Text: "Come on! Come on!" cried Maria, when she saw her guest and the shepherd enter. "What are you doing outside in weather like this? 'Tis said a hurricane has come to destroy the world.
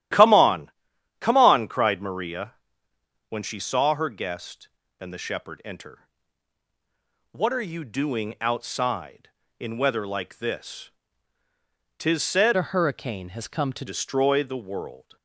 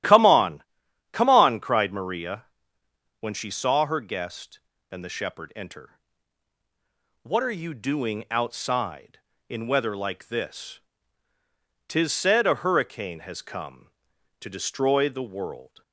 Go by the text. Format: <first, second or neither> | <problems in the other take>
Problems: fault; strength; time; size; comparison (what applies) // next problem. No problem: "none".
second | starts louder than the rest; strong; until 1.6 s; 13 dB; strong in the second // changes voice from "a" to "to"; from 12.5 to 13.8 s; 1.3 s long